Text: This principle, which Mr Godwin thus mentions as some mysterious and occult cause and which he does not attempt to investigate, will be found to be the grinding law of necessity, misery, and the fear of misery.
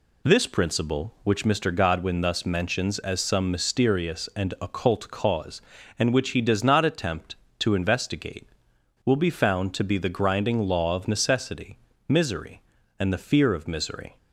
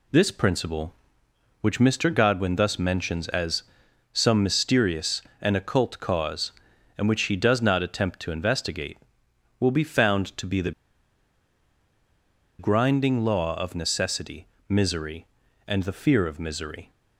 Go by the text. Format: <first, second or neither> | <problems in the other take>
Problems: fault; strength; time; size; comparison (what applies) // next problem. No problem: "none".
first | pauses between "as" and "some"; noticeable; at 3.6 s; 0.50 s long // pauses between "the" and "grinding"; strong; at 10.7 s; 1.8 s long